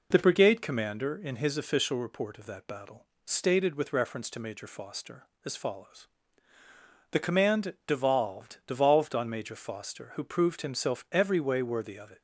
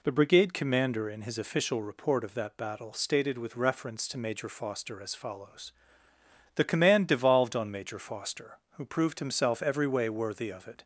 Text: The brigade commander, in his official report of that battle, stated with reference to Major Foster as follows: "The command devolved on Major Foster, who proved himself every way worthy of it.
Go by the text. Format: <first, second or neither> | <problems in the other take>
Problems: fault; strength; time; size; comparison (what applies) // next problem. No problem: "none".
second | says "devolved" twice; at 8.6 s